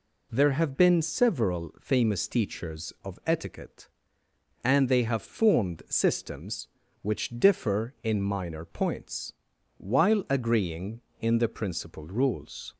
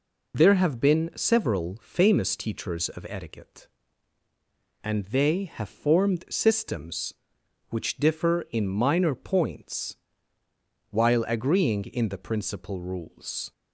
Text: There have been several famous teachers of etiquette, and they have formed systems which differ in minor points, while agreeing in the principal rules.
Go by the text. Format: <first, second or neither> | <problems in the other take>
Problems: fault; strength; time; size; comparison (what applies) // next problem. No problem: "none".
neither | none